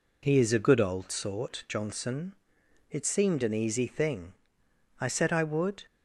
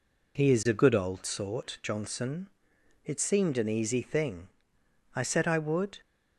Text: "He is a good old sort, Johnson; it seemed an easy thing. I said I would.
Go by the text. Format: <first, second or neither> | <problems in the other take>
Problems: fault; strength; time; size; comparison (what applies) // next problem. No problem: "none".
neither | none